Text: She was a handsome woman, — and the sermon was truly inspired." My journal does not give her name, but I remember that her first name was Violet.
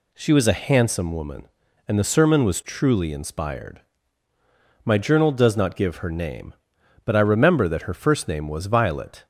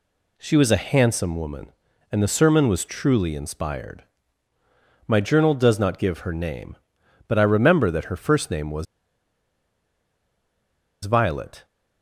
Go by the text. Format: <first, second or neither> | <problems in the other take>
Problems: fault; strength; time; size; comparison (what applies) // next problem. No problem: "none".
first | pauses between "was" and "Violet"; strong; at 8.8 s; 2.1 s long